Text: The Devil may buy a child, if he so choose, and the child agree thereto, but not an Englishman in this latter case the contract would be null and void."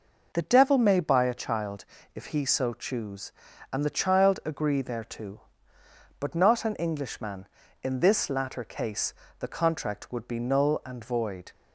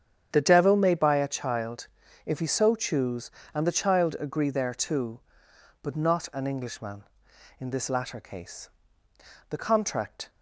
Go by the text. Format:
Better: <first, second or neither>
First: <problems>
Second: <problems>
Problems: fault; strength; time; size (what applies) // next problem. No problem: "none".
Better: first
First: pauses between "case" and "the"; slight; at 9.1 s; 0.28 s long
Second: starts louder than the rest; strong; until 1.3 s; 8 dB // pauses between "case" and "the"; noticeable; at 8.6 s; 0.80 s long // stops before "would be null and void"; at 10.2 s